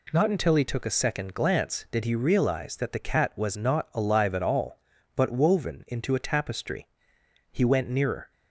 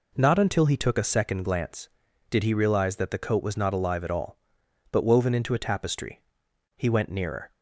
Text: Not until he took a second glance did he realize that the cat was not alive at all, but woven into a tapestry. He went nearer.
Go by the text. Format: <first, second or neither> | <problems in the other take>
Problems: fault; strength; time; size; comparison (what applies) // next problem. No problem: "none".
first | says "coat" for "cat"; at 3.1 s